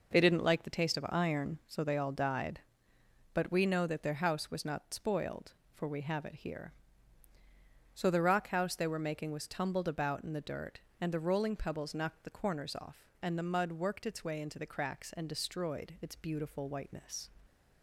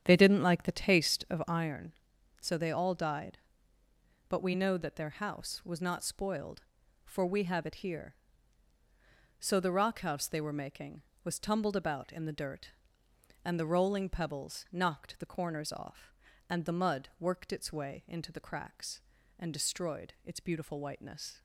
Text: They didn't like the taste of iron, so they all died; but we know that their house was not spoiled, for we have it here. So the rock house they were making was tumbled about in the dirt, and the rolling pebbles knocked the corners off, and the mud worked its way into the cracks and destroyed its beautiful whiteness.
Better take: first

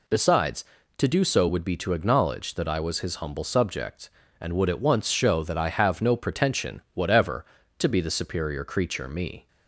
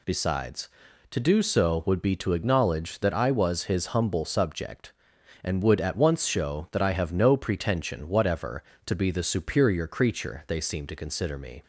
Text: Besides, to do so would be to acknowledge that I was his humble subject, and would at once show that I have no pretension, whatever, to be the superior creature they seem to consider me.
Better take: second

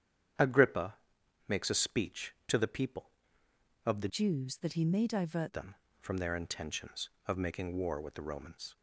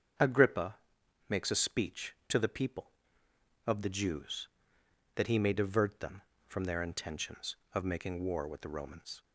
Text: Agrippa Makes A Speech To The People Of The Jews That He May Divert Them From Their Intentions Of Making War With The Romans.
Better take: second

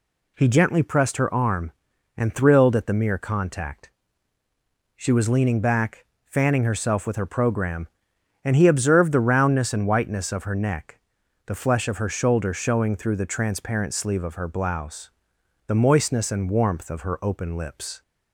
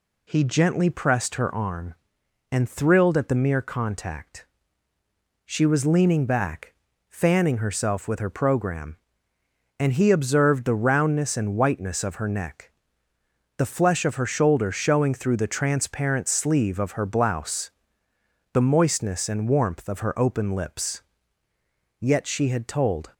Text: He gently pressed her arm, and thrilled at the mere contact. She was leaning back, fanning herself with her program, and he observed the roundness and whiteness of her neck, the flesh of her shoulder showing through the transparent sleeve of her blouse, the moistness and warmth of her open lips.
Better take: first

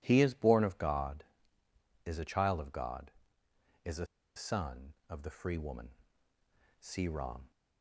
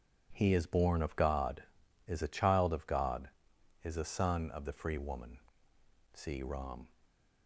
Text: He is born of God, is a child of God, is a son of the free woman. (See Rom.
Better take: second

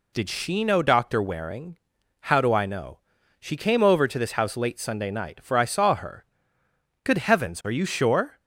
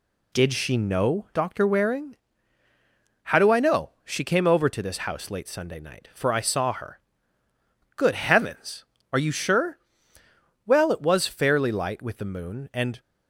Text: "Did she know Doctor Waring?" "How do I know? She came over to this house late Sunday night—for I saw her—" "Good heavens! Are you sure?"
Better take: first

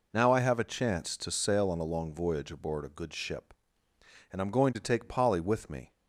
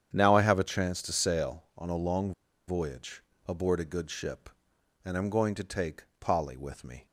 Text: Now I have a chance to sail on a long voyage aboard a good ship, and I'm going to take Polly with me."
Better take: first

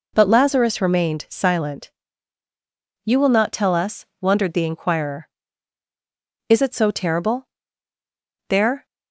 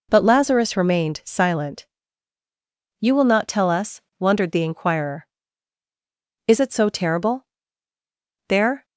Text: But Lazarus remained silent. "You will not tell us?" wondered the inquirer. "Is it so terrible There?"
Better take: neither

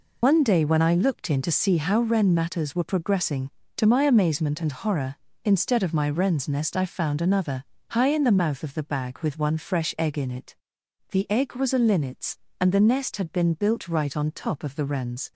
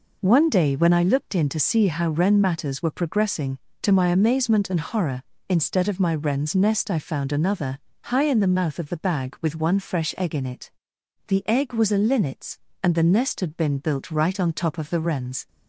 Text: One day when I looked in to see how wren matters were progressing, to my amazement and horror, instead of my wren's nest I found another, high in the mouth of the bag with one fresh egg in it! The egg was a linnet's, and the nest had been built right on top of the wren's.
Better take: second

